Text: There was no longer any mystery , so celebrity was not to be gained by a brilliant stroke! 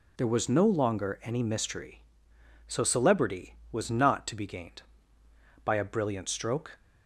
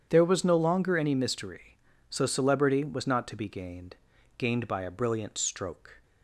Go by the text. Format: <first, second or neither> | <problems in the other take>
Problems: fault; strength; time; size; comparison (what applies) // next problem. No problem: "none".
first | starts louder than the rest; strong; until 1.1 s; 8.5 dB // says "gained" twice; at 4.3 s